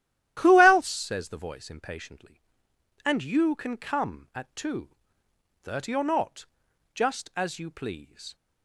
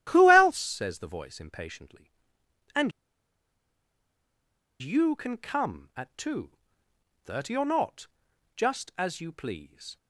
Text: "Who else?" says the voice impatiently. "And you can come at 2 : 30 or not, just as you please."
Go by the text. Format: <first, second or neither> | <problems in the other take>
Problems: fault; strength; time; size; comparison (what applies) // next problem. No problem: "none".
first | starts louder than the rest; strong; until 1.1 s; 12.5 dB; strong in the first // pauses between "And" and "you"; strong; at 2.9 s; 1.9 s long